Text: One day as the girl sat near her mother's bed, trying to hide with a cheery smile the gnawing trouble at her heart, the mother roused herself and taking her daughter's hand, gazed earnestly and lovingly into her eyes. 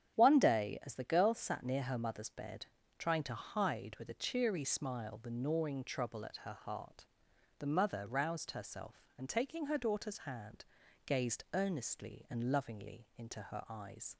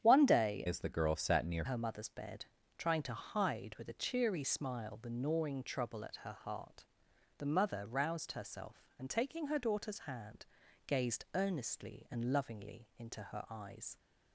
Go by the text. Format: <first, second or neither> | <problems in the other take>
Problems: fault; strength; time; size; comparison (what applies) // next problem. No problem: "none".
first | starts louder than the rest; strong; until 1.0 s; 9 dB; strong in the first // changes voice from "as" to "near"; from 0.6 to 1.6 s; 1.0 s long